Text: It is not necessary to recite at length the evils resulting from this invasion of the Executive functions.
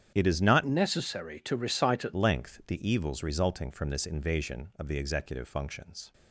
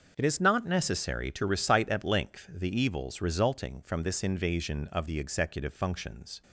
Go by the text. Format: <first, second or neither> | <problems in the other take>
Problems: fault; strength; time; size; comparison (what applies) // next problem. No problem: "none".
second | starts louder than the rest; strong; until 1.1 s; 9 dB; also in the second // changes voice from "necessary" to "at"; from 0.6 to 2.1 s; 1.5 s long